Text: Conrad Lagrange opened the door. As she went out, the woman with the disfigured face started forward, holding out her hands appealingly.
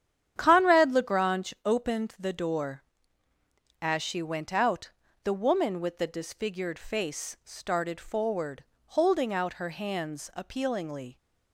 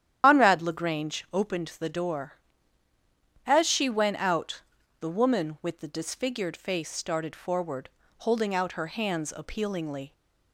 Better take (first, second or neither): first